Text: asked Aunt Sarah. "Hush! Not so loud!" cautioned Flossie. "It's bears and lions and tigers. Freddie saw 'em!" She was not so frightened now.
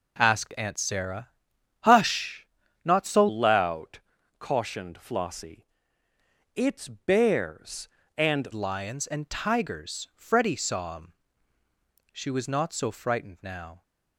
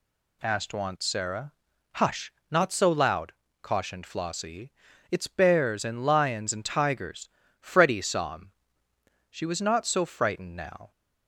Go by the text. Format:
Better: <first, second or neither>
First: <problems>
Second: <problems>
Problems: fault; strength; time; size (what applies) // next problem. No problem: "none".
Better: second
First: changes voice from "loud" to "and"; from 3.2 to 8.4 s; 5.2 s long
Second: none